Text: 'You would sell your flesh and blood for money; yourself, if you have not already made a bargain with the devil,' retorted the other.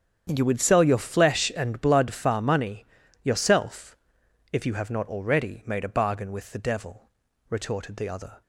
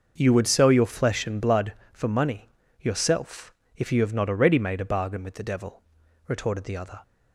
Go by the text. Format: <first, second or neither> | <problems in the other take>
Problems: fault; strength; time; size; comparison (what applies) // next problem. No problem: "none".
second | starts louder than the rest; strong; until 1.3 s; 8.5 dB // says "far" for "for"; at 2.1 s